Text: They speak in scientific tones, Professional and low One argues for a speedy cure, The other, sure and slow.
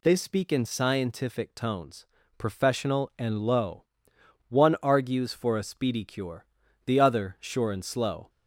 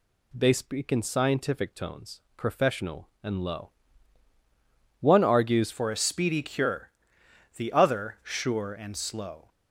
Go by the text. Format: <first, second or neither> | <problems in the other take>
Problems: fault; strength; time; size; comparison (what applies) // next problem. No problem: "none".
first | pauses between "low" and "One"; strong; at 3.7 s; 1.3 s long; noticeable in the first // changes voice at "for"; from 5.7 s on; 3.7 s long